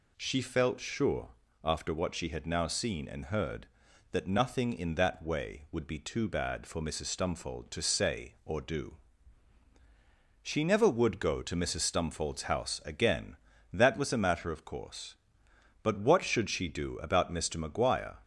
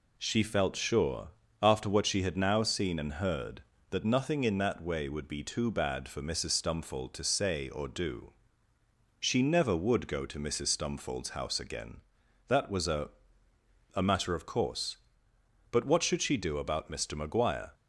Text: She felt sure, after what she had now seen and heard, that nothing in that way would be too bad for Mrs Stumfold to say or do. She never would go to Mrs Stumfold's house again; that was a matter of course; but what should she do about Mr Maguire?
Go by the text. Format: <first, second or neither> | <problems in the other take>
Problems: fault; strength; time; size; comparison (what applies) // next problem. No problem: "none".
first | says "a" twice; at 13.9 s